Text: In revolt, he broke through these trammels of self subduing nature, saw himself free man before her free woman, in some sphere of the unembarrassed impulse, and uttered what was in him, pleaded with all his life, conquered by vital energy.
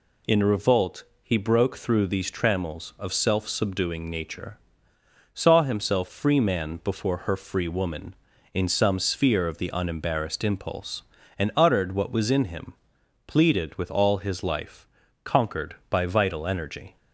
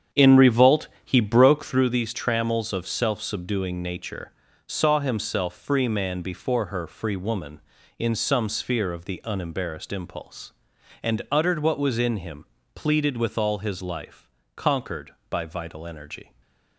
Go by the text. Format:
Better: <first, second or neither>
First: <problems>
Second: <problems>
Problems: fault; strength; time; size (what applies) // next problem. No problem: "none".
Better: first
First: none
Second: starts louder than the rest; strong; until 2.0 s; 8 dB // stays silent after the last word; slight; from 16.2 s on; 0.5 s long